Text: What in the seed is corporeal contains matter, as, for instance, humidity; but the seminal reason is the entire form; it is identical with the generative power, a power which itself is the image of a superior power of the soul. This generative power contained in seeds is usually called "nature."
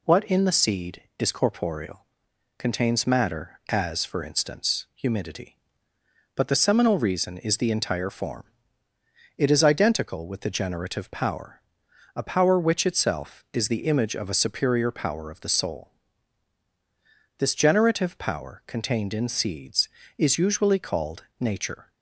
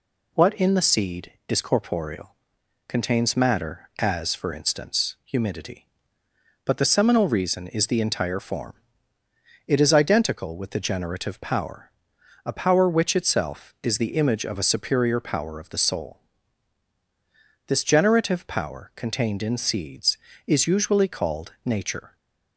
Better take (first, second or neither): neither